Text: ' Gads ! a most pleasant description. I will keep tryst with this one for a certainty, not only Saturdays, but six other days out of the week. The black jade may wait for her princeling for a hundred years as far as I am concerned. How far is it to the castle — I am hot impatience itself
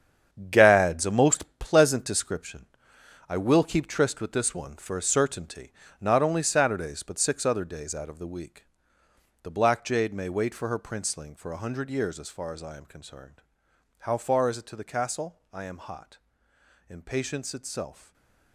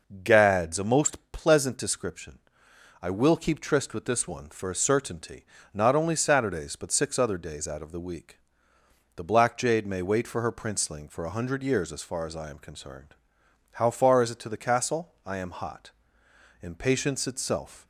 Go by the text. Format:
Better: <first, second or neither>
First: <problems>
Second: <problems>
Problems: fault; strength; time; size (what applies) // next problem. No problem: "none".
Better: second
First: gets quieter; strong; throughout; 8.5 dB // pauses between "hot" and "impatience"; noticeable; at 16.1 s; 0.70 s long // stays silent after the last word; slight; from 17.9 s on; 0.6 s long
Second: pauses between "hot" and "impatience"; noticeable; at 15.9 s; 0.70 s long